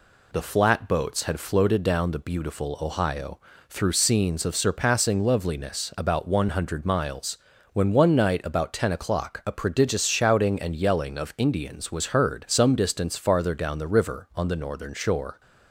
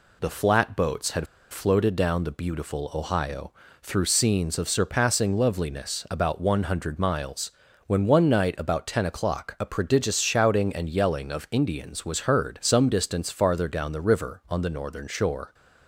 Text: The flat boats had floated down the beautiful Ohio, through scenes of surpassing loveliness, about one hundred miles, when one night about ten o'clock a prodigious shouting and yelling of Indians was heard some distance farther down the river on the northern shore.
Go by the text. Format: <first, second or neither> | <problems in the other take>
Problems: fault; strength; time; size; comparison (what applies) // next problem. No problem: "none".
first | pauses between "had" and "floated"; slight; at 1.2 s; 0.27 s long